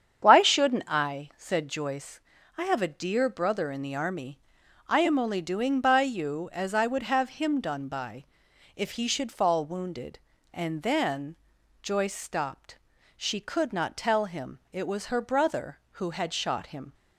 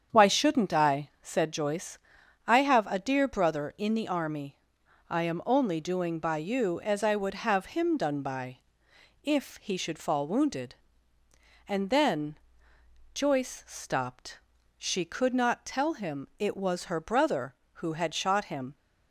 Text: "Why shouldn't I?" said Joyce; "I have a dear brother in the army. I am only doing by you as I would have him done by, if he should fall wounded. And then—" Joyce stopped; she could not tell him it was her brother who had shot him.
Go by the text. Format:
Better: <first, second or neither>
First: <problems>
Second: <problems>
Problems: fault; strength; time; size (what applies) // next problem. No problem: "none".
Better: neither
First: starts louder than the rest; strong; until 1.2 s; 8 dB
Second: starts louder than the rest; strong; until 1.2 s; 8 dB